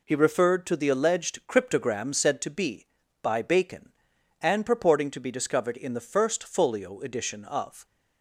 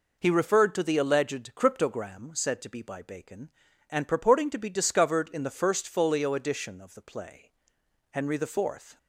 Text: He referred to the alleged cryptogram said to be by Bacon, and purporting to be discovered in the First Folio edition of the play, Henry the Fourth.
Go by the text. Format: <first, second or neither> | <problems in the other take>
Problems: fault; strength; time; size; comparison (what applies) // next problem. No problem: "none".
second | stops before "the play Henry the Fourth"; at 7.8 s